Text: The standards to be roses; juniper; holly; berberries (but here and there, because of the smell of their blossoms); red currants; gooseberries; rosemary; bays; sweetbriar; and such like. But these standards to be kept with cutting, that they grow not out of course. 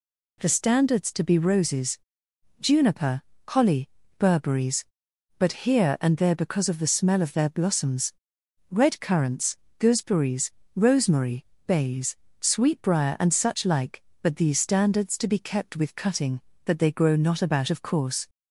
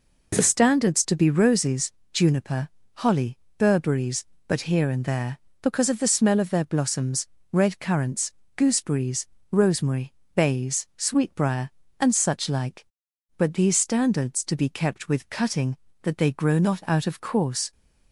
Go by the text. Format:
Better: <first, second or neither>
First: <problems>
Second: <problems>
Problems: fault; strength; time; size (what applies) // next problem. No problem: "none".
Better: second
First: says "about" for "out"; at 17.4 s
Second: none